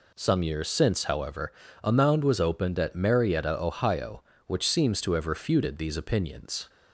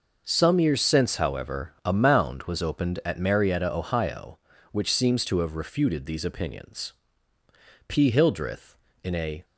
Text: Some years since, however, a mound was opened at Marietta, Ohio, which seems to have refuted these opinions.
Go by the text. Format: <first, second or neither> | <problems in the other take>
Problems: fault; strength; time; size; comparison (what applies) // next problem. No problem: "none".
first | goes on to say "P Hildreth in a"; from 7.8 s on; 1.5 s long